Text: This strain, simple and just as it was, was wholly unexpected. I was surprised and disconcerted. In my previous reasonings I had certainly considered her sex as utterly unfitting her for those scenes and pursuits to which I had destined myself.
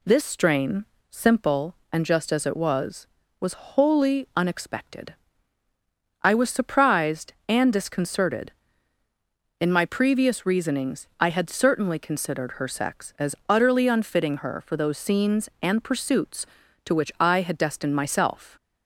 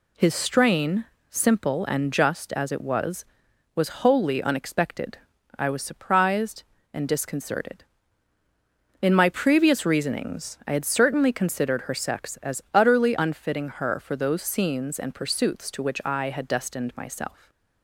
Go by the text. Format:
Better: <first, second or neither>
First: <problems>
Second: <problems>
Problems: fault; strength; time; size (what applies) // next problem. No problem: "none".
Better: first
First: none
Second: says "His" for "This"; at 0.1 s // stays silent after the last word; slight; from 17.3 s on; 0.5 s long